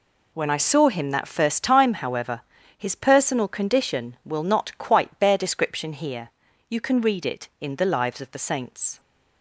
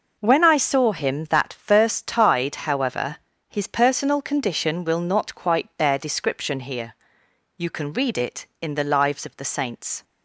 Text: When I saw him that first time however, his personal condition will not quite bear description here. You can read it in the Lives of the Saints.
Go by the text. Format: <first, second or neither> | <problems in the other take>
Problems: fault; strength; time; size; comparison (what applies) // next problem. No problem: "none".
first | says "tide" for "time"; at 2.0 s